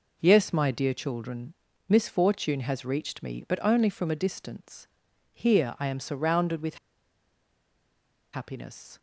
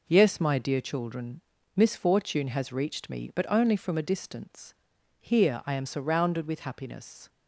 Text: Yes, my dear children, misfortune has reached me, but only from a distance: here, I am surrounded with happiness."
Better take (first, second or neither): second